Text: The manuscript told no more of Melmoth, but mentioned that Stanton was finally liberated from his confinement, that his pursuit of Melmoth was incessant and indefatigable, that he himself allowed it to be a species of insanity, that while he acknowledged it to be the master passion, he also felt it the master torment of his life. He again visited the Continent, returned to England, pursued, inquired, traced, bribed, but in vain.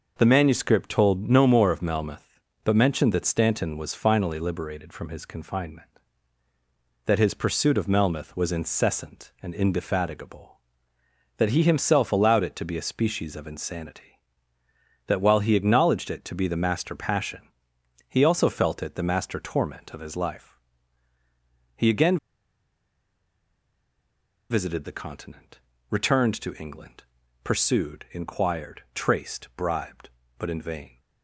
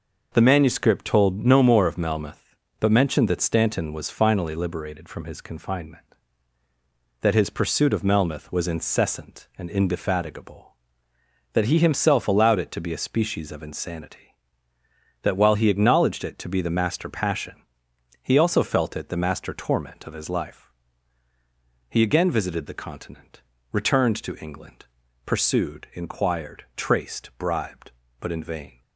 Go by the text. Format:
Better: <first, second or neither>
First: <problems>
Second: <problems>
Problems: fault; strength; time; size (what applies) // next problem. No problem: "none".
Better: second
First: pauses between "again" and "visited"; strong; at 22.1 s; 2.3 s long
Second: none